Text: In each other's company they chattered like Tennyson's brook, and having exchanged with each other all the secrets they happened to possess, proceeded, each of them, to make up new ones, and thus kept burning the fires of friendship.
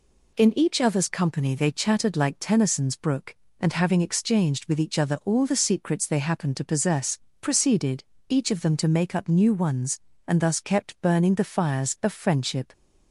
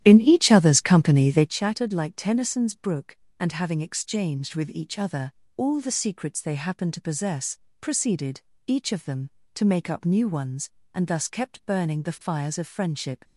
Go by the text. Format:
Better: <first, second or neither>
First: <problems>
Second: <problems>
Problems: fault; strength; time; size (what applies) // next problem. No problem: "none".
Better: first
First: none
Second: starts louder than the rest; strong; until 1.5 s; 12 dB // pauses between "other" and "all"; slight; at 5.3 s; 0.24 s long